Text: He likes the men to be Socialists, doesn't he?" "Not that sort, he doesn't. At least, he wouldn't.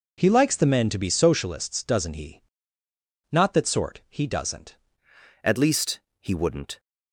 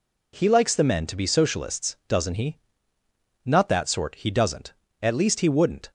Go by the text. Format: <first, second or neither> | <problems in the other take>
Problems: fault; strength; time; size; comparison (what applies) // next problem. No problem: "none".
second | changes voice at "At"; from 5.4 s on; 1.3 s long